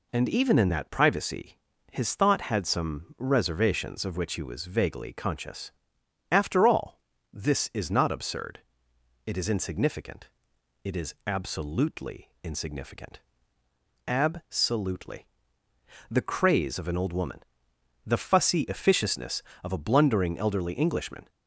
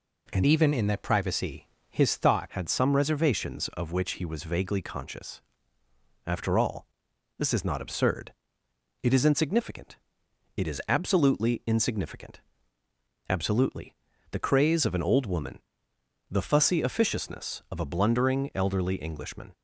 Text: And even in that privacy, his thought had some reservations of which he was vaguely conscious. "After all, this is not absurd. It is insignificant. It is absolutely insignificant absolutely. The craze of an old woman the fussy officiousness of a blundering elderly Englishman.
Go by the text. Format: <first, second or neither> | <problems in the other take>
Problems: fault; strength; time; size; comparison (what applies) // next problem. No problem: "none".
first | changes voice from "even" to "thought"; from 0.4 to 2.5 s; 2.1 s long // pauses between "insignificant" and "absolutely"; noticeable; at 12.4 s; 0.86 s long; noticeable in the first // pauses between "woman" and "the"; noticeable; at 15.5 s; 0.72 s long; noticeable in the first